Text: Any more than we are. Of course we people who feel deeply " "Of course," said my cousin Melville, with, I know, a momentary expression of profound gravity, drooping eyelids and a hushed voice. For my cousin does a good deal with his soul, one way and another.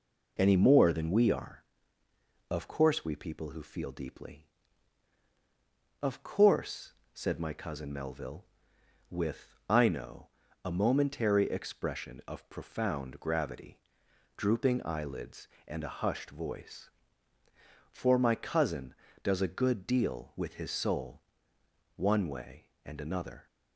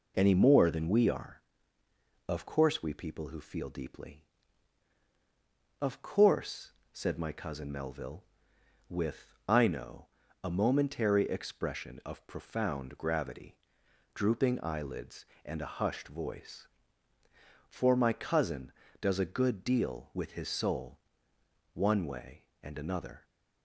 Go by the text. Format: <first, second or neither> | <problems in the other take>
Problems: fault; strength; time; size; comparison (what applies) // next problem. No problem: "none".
neither | none